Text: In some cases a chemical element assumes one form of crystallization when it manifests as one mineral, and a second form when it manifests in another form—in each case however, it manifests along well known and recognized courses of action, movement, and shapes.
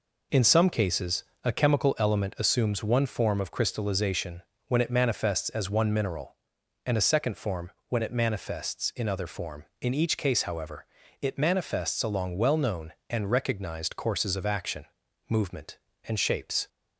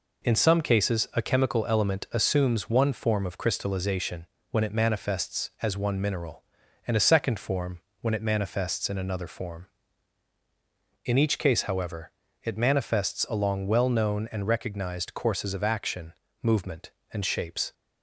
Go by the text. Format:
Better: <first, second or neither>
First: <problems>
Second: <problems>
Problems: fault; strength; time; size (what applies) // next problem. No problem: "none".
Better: second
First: pauses between "cases" and "a"; slight; at 1.2 s; 0.18 s long // pauses between "crystallization" and "when"; slight; at 4.4 s; 0.26 s long // pauses between "form" and "when"; slight; at 7.7 s; 0.16 s long // says "other" for "another"; at 9.0 s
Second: pauses between "crystallization" and "when"; slight; at 4.2 s; 0.26 s long // pauses between "form" and "when"; slight; at 7.8 s; 0.20 s long